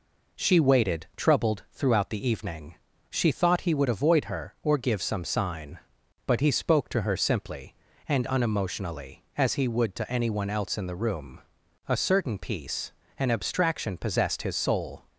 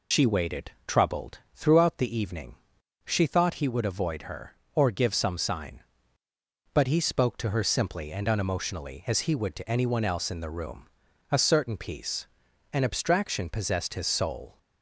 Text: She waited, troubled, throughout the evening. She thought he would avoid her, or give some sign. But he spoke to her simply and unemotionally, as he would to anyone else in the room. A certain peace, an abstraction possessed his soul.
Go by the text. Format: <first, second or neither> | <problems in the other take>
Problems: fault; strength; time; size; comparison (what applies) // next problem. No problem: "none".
first | loses the start of "She"; at 0.1 s; 70 ms